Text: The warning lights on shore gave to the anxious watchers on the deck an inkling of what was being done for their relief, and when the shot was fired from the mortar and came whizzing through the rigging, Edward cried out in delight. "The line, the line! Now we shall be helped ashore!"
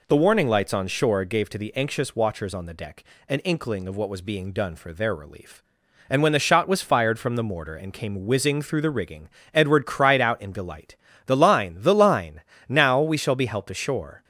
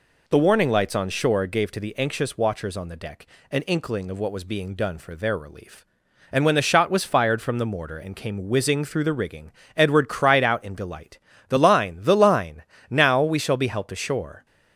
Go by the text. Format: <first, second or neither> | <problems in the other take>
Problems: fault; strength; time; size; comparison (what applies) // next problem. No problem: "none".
neither | pauses between "deck" and "an"; slight; the same in both